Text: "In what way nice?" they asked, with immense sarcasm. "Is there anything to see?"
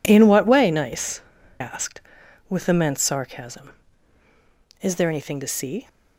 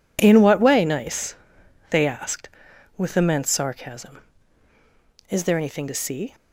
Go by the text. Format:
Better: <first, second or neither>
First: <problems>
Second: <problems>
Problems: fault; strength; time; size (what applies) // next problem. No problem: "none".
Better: second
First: skips "they"; at 1.3 s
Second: none